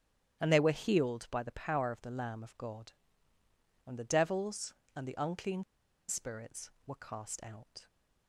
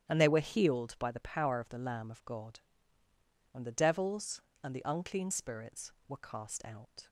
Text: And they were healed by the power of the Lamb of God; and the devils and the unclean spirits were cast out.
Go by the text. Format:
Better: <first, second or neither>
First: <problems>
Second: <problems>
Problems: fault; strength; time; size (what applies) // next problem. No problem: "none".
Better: second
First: starts louder than the rest; strong; until 1.4 s; 10.5 dB // pauses between "unclean" and "spirits"; noticeable; at 5.6 s; 0.46 s long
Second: starts louder than the rest; strong; until 1.1 s; 10 dB